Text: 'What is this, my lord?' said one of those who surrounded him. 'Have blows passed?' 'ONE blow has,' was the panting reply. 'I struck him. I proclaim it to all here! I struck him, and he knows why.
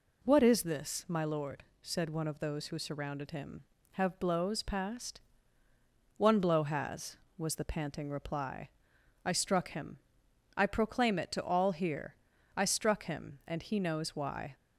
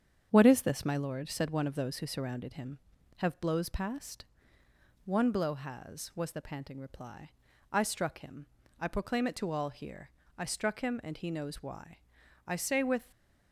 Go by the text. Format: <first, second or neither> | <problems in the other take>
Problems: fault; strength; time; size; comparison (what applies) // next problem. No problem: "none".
first | starts louder than the rest; strong; until 1.3 s; 8 dB // goes on to say "I say with"; noticeable; from 12.4 s on; 0.64 s long